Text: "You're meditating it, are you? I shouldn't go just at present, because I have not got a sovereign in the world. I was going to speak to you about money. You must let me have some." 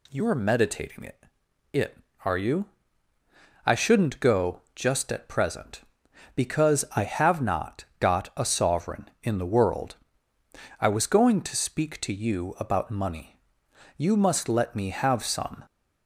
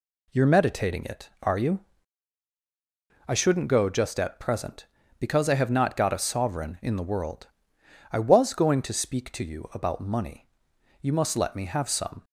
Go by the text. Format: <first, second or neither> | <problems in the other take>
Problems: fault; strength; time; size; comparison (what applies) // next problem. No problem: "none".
second | says "it" twice; at 1.7 s // pauses between "go" and "just"; slight; at 4.6 s; 0.16 s long